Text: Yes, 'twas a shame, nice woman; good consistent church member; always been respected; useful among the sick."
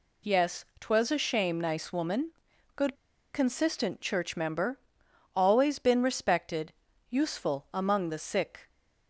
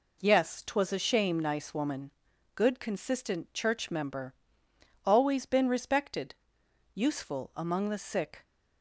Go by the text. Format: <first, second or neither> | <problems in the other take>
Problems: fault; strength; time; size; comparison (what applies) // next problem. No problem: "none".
second | pauses between "good" and "consistent"; at 2.9 s; 0.37 s long